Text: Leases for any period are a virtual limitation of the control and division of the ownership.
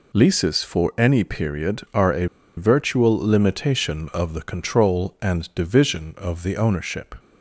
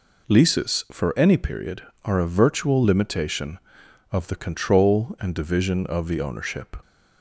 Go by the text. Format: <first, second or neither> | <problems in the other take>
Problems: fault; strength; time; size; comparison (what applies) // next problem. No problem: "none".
second | pauses between "a" and "virtual"; slight; at 2.2 s; 0.30 s long